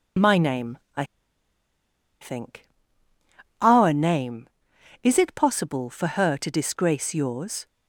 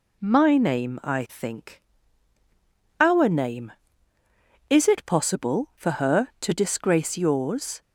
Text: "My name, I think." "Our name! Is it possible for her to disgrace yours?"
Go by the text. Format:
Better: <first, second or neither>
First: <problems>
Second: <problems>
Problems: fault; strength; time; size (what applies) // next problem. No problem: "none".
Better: second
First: pauses between "I" and "think"; at 1.0 s; 1.1 s long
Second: none